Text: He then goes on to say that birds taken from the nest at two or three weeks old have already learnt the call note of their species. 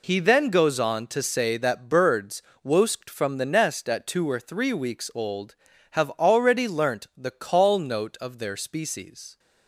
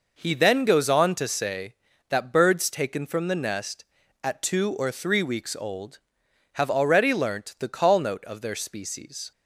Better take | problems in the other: second | says "wosked" for "taken"; at 2.6 s

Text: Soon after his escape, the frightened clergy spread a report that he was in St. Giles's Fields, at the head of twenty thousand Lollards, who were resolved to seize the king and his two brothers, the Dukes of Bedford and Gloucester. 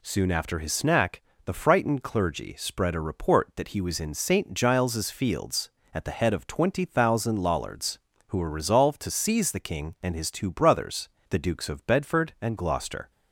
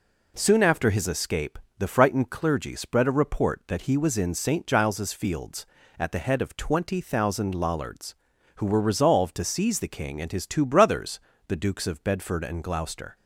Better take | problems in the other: second | says "snack" for "escape"; at 0.7 s

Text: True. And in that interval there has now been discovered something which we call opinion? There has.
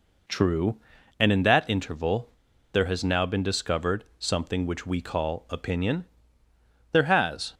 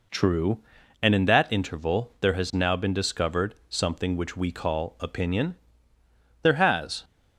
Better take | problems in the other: second | pauses between "interval" and "there"; at 2.2 s; 0.43 s long

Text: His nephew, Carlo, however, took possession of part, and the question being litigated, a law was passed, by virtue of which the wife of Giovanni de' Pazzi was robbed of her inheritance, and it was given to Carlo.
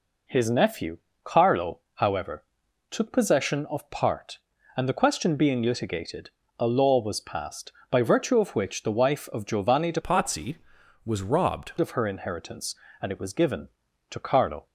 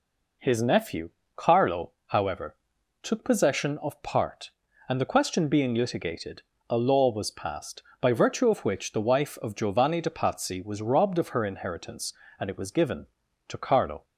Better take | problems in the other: second | changes voice from "Pazzi" to "robbed"; from 9.9 to 11.7 s; 1.8 s long

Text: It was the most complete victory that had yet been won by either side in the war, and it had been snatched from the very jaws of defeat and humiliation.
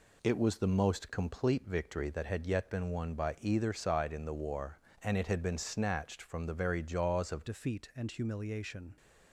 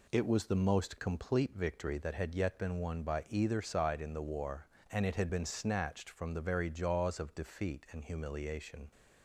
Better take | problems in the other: second | changes voice at "defeat"; from 7.4 s on; 1.5 s long

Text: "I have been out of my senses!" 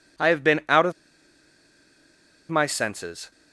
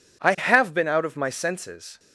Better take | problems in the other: second | pauses between "of" and "my"; strong; at 0.9 s; 1.5 s long

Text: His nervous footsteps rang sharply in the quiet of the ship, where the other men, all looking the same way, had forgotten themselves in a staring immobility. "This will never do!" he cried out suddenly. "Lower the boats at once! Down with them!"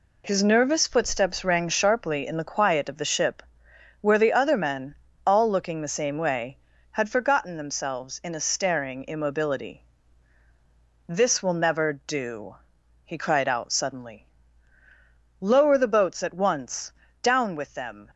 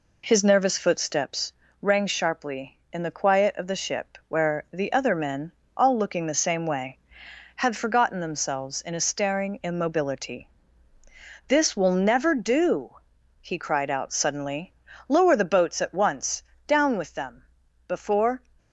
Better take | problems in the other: first | pauses between "footsteps" and "rang"; slight; at 1.5 s; 0.30 s long // goes on to say "Before"; from 17.8 s on; 0.54 s long

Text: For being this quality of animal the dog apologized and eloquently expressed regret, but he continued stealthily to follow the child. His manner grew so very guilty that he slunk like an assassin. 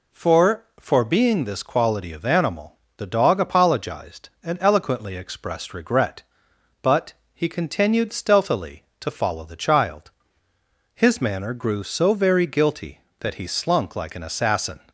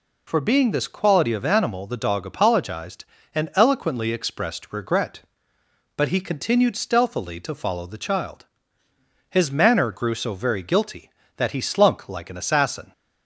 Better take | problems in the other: second | says "For" twice; at 0.7 s // pauses between "animal" and "the"; slight; at 2.7 s; 0.22 s long // pauses between "but" and "he"; slight; at 7.1 s; 0.20 s long

